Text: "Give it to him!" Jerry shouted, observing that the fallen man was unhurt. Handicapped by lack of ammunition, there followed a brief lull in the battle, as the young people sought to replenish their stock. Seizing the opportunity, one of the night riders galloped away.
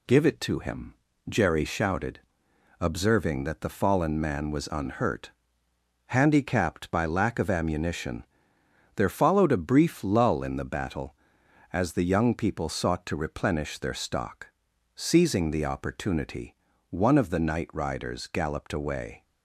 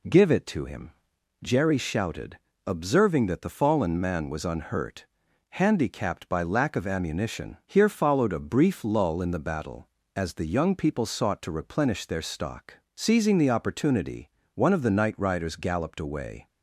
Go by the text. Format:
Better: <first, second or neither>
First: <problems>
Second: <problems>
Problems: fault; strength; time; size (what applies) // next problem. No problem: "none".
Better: first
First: none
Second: says "here" for "there"; at 7.6 s